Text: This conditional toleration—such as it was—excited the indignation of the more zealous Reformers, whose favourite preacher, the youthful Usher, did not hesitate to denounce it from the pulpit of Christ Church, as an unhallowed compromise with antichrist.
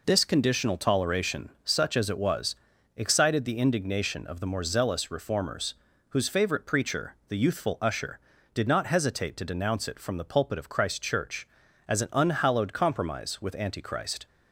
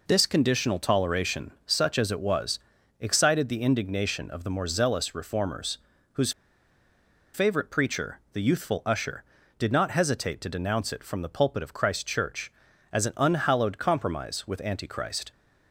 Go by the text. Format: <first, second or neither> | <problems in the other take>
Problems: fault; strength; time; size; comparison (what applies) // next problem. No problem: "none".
first | pauses between "whose" and "favourite"; at 6.3 s; 1.0 s long